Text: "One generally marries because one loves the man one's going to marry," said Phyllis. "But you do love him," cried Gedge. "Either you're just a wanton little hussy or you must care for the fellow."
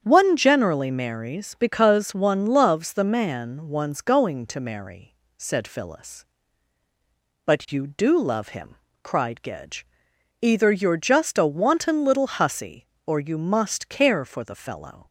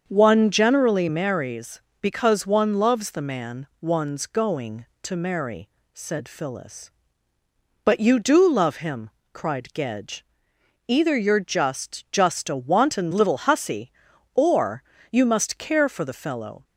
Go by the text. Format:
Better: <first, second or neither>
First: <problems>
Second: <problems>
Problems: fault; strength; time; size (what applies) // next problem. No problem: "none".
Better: first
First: starts louder than the rest; strong; until 1.0 s; 8.5 dB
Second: starts louder than the rest; until 1.0 s; 7 dB // says "just" twice; at 12.1 s // pauses between "or" and "you"; slight; at 14.8 s; 0.30 s long